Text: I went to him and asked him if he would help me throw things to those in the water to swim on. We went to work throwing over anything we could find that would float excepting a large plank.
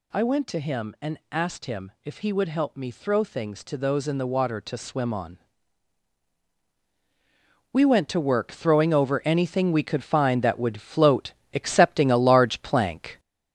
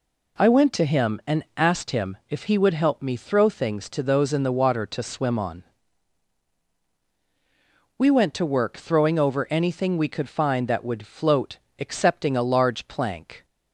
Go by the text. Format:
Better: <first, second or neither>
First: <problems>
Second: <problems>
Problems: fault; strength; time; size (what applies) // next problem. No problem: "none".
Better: second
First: gets louder; noticeable; throughout; 5 dB // pauses between "float" and "excepting"; slight; at 11.3 s; 0.22 s long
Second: pauses between "float" and "excepting"; slight; at 11.5 s; 0.22 s long